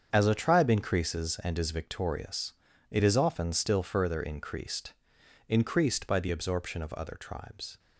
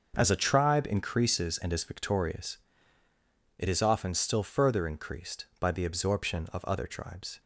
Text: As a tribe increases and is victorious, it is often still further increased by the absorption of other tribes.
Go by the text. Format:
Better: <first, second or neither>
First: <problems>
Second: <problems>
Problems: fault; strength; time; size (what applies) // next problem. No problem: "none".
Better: second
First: starts louder than the rest; strong; until 1.1 s; 7 dB // says "increased" twice; at 5.4 s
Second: starts louder than the rest; until 1.1 s; 6 dB